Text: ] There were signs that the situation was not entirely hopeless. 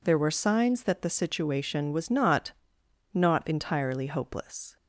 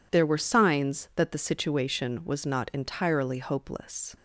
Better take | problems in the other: second | says "not" twice; at 3.1 s

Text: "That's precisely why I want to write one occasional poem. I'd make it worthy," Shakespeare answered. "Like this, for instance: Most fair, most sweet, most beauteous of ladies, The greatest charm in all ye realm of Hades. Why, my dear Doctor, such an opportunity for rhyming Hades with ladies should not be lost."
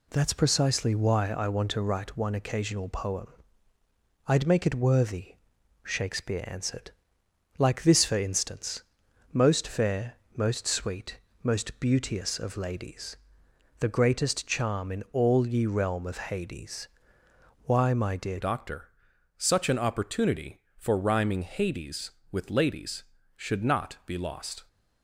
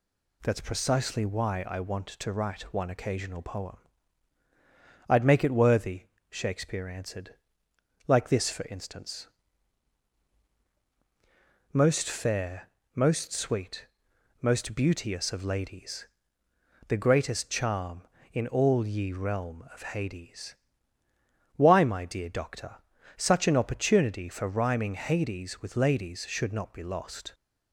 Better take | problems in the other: second | changes voice at "Doctor"; from 18.4 s on; 6.2 s long

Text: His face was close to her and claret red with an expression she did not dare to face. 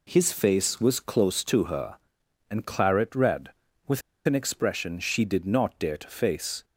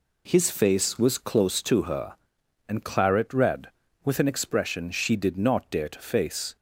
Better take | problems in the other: second | pauses between "with" and "an"; slight; at 4.0 s; 0.24 s long

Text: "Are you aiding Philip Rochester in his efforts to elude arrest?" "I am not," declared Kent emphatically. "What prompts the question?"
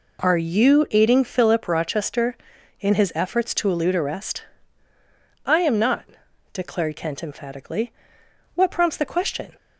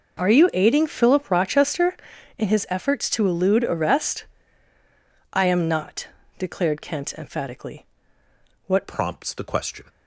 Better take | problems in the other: first | changes voice at "prompts"; from 8.8 s on; 1.0 s long

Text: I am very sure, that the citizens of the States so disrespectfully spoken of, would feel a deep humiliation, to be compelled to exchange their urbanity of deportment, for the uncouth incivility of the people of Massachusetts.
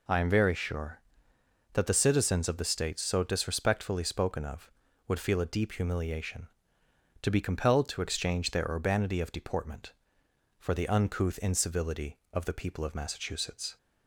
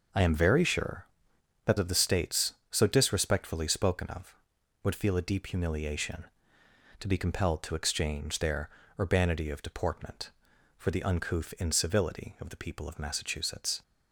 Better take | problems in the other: first | starts louder than the rest; until 1.7 s; 6 dB // skips "the citizens"; at 1.7 s // pauses between "their" and "urbanity"; slight; at 8.6 s; 0.28 s long

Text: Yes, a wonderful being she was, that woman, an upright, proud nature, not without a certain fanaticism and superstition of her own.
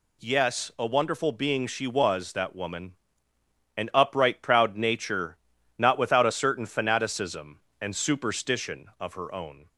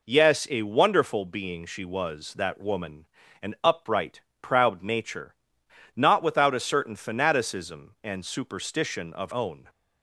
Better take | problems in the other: first | skips "her"; at 9.3 s

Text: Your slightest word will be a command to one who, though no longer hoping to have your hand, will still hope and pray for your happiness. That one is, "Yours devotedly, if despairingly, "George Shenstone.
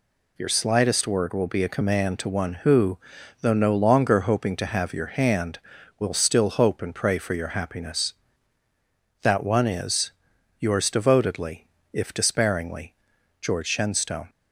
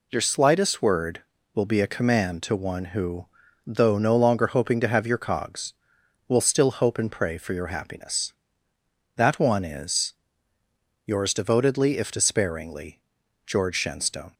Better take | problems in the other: first | says "cogs" for "hand"; at 5.1 s

